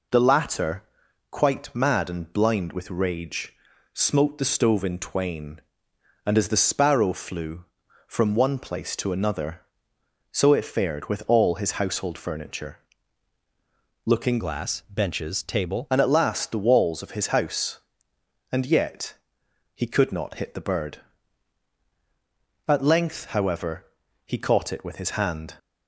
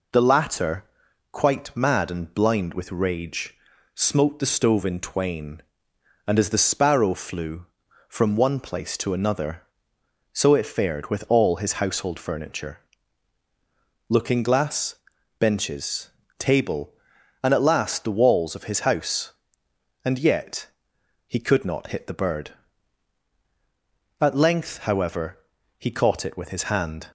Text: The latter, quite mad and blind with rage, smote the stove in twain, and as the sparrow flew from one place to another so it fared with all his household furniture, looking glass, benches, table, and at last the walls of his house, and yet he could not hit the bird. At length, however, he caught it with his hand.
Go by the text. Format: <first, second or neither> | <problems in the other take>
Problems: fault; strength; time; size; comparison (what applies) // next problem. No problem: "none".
second | changes voice from "glass" to "table"; from 14.3 to 15.8 s; 1.5 s long // pauses between "yet" and "he"; noticeable; at 19.1 s; 0.60 s long; noticeable in the second